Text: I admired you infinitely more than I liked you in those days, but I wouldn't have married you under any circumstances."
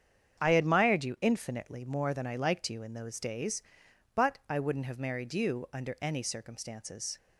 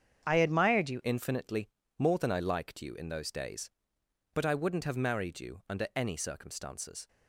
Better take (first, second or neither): first